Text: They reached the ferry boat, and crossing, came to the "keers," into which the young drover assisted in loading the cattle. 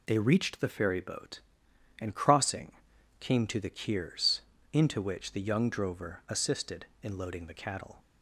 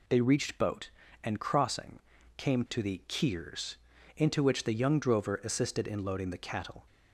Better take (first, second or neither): first